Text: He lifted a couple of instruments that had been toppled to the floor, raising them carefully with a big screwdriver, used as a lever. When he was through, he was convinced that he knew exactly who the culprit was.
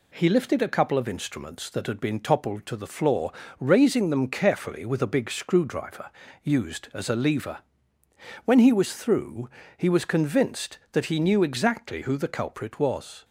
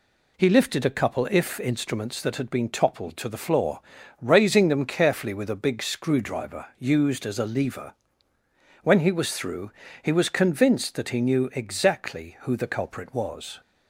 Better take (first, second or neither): first